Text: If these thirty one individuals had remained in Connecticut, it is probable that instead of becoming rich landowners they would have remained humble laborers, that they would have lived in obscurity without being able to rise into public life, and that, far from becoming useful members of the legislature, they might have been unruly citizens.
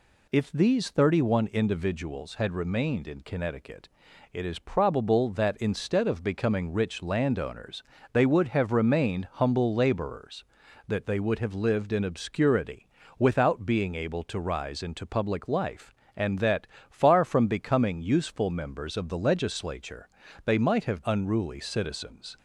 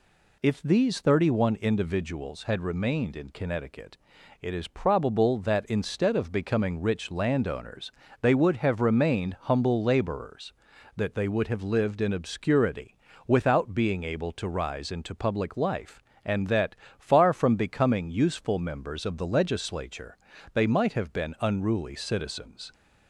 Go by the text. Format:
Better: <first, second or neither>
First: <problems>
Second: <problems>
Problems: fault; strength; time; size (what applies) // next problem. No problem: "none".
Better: second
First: pauses between "landowners" and "they"; slight; at 7.8 s; 0.30 s long // pauses between "obscurity" and "without"; slight; at 12.8 s; 0.30 s long // skips "been"; at 21.0 s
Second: pauses between "landowners" and "they"; slight; at 7.9 s; 0.30 s long // pauses between "obscurity" and "without"; slight; at 12.9 s; 0.30 s long